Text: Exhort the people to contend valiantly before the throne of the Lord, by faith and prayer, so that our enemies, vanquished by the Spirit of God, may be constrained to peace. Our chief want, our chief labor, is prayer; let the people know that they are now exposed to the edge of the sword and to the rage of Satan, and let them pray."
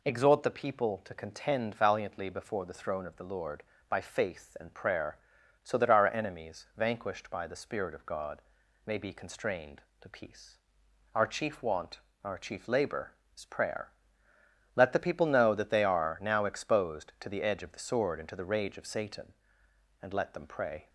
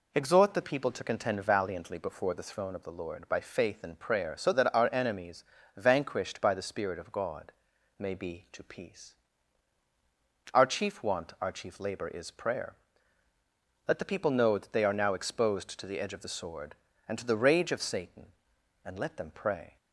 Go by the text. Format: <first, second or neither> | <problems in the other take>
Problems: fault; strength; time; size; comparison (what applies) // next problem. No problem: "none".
first | skips "constrained"; at 8.4 s